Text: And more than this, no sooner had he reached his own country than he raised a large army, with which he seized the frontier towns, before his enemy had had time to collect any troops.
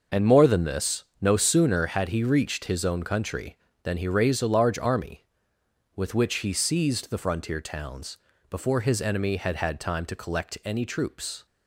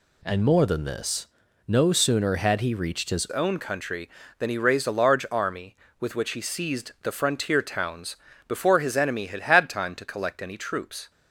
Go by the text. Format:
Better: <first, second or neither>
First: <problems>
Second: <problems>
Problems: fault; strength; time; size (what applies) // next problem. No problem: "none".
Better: first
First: none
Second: changes voice at "own"; from 3.2 s on; 7.8 s long